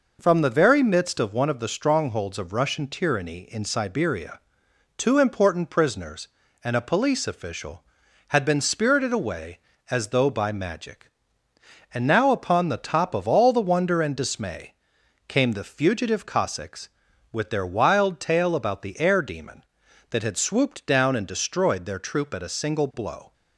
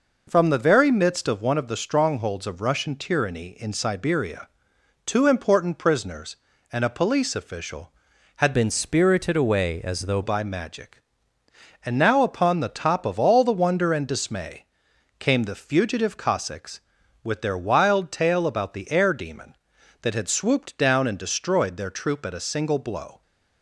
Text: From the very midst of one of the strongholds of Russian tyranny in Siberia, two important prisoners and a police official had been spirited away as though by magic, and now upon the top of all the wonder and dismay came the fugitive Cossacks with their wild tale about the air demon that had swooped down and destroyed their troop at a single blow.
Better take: first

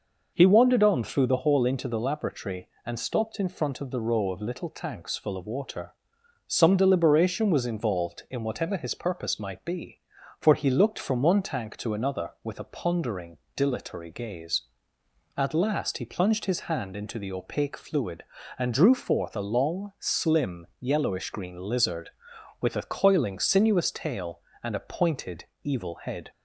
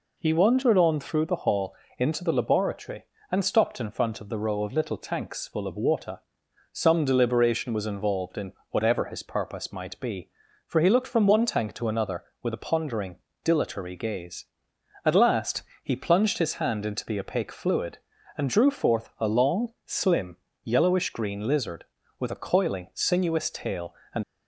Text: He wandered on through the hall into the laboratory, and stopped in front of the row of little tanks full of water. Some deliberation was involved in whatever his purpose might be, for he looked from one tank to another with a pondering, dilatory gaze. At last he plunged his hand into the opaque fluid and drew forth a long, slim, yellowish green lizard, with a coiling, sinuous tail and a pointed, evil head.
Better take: first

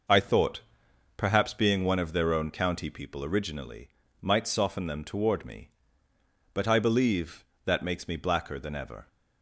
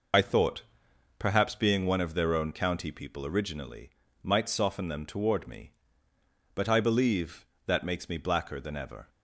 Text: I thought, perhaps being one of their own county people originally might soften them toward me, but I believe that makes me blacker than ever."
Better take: first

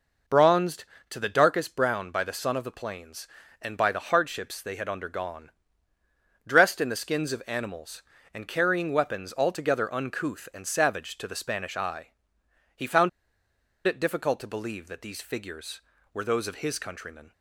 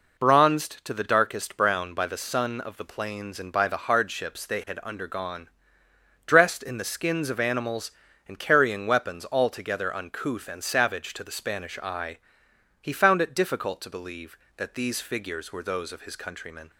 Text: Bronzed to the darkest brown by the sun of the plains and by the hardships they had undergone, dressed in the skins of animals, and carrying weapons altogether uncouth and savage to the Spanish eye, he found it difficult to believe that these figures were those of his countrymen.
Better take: second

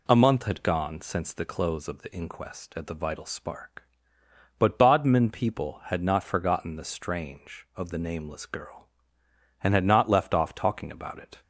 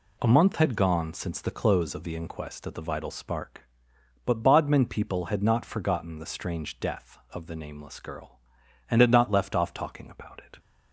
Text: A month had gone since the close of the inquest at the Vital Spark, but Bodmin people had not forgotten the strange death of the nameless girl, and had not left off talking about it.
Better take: second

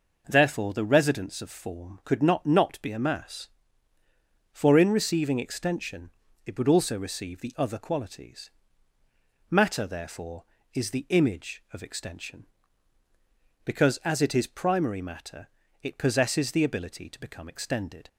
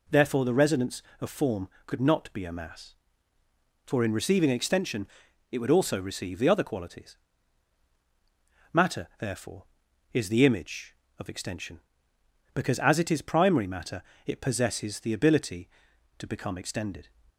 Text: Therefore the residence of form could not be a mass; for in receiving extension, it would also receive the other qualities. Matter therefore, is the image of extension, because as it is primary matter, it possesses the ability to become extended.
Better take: second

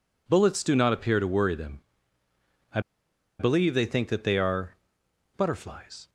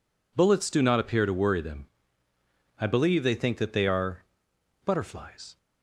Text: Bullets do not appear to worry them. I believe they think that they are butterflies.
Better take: second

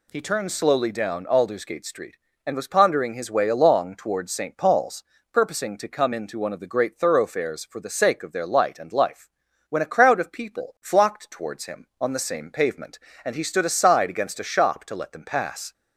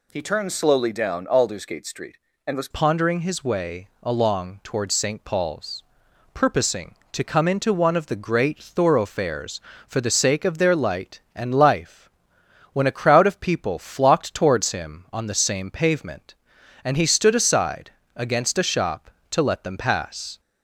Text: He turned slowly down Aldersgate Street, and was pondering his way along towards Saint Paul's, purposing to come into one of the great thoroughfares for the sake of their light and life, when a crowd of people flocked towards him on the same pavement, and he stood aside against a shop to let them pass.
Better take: first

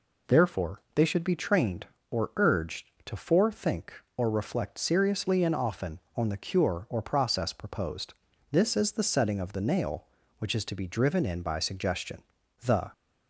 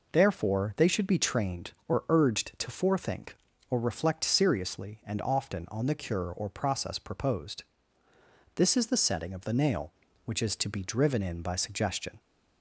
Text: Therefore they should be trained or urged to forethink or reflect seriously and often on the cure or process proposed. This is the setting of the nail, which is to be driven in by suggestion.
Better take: second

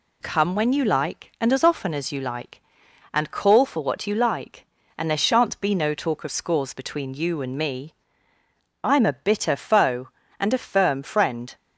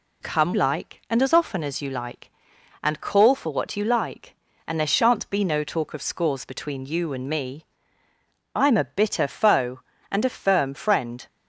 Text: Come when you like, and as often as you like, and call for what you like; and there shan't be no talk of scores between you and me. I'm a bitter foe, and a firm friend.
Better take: first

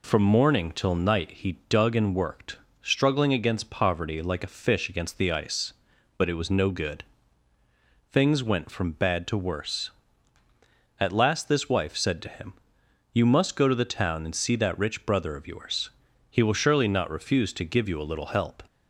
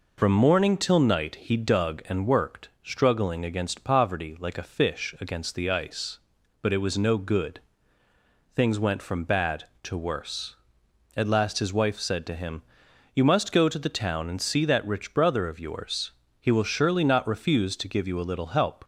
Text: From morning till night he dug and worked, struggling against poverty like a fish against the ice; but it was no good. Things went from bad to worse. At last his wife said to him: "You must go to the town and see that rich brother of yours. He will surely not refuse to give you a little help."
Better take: second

